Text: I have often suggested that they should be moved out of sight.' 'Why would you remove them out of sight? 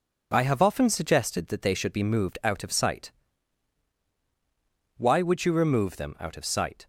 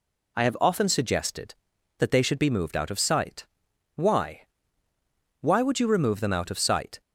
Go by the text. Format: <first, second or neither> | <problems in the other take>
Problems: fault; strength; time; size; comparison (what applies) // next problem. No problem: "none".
first | says "Why" twice; at 5.4 s